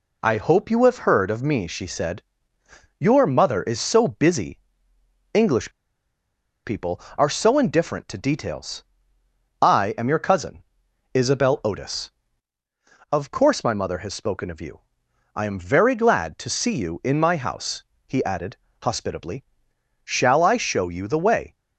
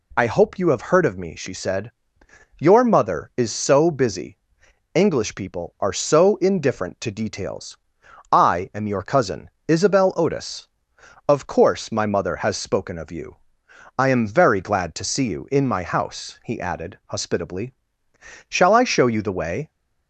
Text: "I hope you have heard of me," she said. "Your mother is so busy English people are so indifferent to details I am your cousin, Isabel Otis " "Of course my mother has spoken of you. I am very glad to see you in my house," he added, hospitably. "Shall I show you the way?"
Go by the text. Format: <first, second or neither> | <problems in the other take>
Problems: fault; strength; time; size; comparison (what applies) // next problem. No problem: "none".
second | pauses between "busy" and "English"; noticeable; at 4.5 s; 0.76 s long; noticeable in the second // pauses between "English" and "people"; noticeable; at 5.7 s; 0.94 s long // pauses between "details" and "I"; noticeable; at 8.8 s; 0.76 s long; noticeable in the second